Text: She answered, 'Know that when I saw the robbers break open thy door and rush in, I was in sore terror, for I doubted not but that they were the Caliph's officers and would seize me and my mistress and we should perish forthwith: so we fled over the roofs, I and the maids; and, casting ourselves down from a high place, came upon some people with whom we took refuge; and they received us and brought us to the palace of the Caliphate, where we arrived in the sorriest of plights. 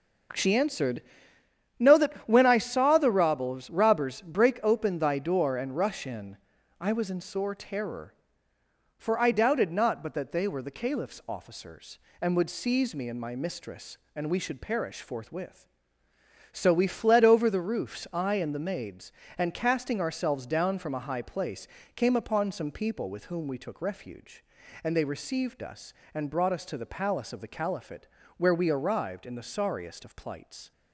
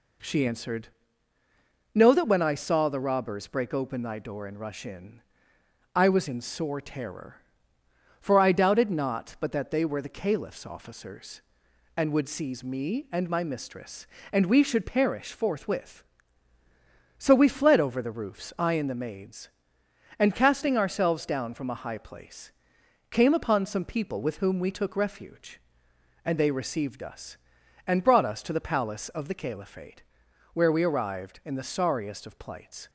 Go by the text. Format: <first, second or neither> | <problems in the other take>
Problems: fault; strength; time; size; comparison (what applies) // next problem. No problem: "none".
second | says "robbers" twice; at 3.6 s